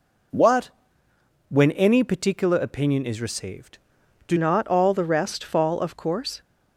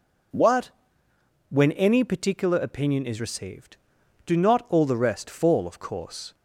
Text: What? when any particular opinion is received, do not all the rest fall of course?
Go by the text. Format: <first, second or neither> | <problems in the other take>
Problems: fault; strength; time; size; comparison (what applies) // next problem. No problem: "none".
second | changes voice at "not"; from 4.3 s on; 2.1 s long